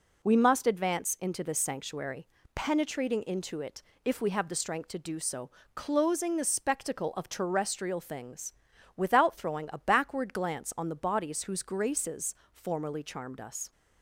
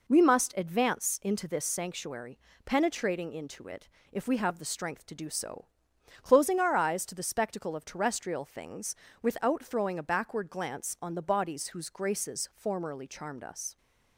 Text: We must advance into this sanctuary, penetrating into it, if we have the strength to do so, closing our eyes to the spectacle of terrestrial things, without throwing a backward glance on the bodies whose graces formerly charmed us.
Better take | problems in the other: second | skips "our eyes to"; at 6.3 s // pauses between "graces" and "formerly"; slight; at 12.3 s; 0.18 s long

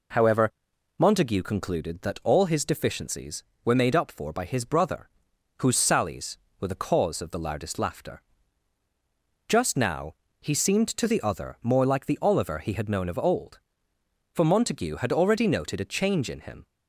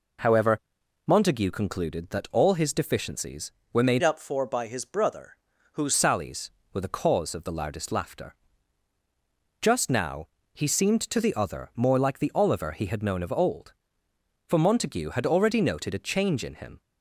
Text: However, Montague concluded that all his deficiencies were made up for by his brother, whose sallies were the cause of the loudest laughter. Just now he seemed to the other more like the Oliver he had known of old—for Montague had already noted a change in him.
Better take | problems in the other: first | changes voice from "up" to "whose"; from 4.0 to 5.9 s; 1.9 s long // pauses between "now" and "he"; slight; at 10.2 s; 0.26 s long; slight in the first

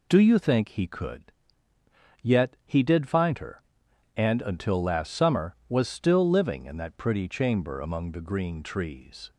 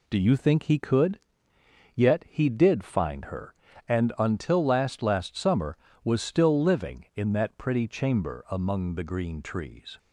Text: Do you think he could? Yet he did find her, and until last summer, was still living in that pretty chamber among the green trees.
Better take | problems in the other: first | says "last" twice; at 5.0 s

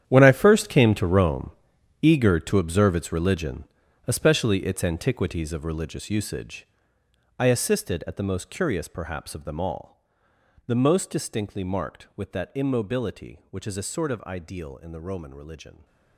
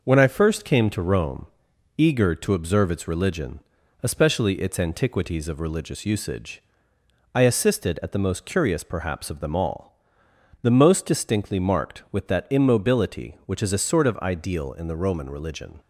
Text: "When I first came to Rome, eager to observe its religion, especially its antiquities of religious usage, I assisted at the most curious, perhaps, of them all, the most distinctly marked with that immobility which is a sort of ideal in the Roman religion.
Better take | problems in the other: second | gets quieter; strong; throughout; 15 dB

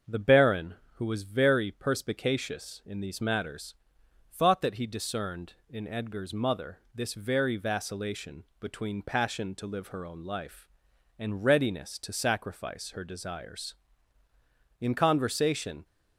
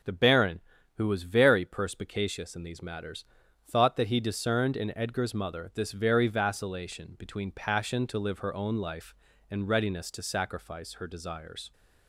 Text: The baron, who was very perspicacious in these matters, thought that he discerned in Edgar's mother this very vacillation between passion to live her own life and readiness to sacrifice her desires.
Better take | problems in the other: second | starts louder than the rest; until 1.2 s; 6.5 dB // pauses between "vacillation" and "between"; slight; at 8.4 s; 0.16 s long // goes on to say "In conversation"; noticeable; from 14.8 s on; 1.0 s long

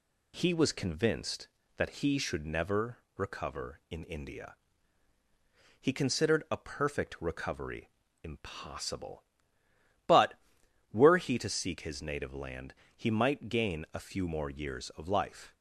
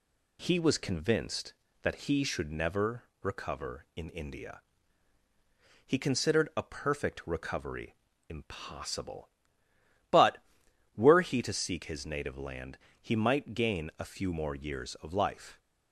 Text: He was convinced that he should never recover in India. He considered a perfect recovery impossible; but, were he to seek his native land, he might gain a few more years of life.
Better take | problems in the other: neither | pauses between "never" and "recover"; slight; the same in both // pauses between "recovery" and "impossible"; slight; the same in both

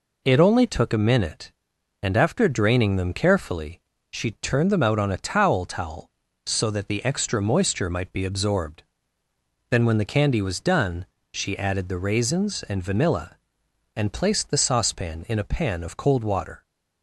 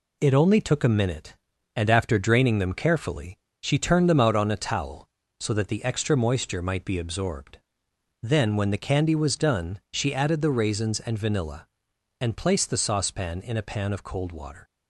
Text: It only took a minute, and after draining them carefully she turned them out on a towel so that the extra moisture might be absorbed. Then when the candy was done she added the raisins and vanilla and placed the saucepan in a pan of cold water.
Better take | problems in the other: second | pauses between "carefully" and "she"; slight; at 3.8 s; 0.32 s long; slight in the second // says "towel" twice; at 5.6 s // pauses between "done" and "she"; slight; at 11.0 s; 0.26 s long

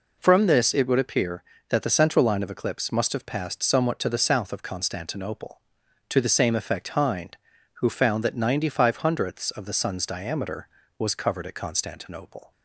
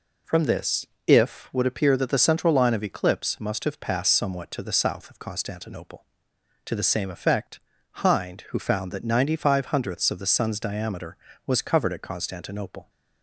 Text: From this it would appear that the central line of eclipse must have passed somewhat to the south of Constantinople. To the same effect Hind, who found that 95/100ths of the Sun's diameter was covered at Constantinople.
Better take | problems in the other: first | says "if" for "it"; at 1.0 s // pauses between "effect" and "Hind"; at 7.5 s; 0.40 s long

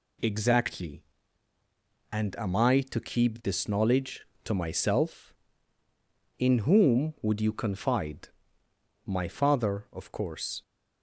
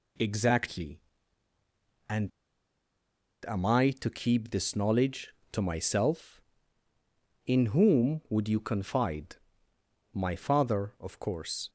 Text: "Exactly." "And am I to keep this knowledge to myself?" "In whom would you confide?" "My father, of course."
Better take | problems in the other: first | pauses between "And" and "am"; at 2.2 s; 1.1 s long

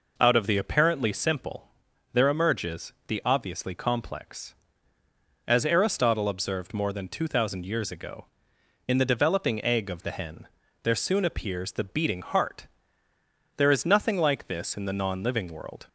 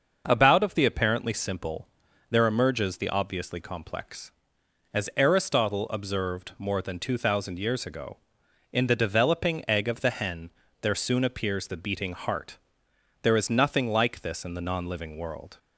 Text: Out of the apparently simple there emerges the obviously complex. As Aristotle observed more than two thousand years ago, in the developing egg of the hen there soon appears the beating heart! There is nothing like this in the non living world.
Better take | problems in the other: first | says "About" for "Out"; at 0.2 s // pauses between "simple" and "there"; at 1.8 s; 0.44 s long; noticeable in the first // pauses between "hen" and "there"; slight; at 10.4 s; 0.32 s long; slight in the first

